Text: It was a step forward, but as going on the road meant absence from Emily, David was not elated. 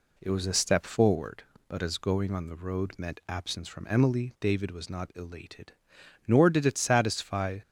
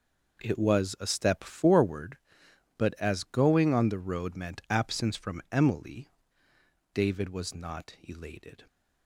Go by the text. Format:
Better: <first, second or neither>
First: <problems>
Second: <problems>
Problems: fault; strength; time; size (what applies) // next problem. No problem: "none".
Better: second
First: goes on to say "Nor did it satisfy"; from 6.2 s on; 1.3 s long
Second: none